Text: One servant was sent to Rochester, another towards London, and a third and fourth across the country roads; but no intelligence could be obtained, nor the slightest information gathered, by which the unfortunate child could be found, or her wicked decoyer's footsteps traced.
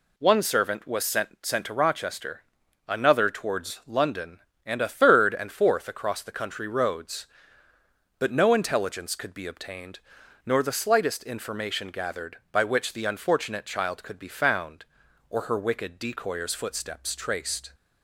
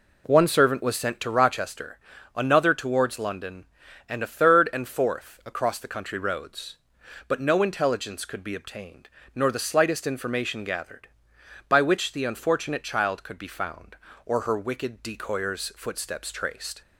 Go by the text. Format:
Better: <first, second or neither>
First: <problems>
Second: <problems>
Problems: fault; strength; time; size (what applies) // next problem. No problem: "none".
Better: second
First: says "sent" twice; at 1.4 s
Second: none